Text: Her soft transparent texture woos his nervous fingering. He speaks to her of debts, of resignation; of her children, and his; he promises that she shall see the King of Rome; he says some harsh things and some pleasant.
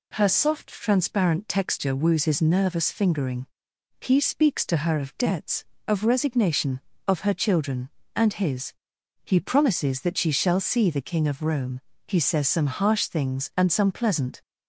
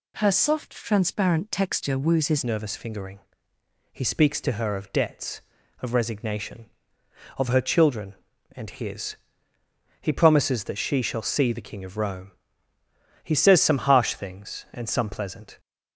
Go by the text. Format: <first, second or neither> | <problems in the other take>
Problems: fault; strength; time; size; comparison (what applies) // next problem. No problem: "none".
first | changes voice at "nervous"; from 2.4 s on; 13.1 s long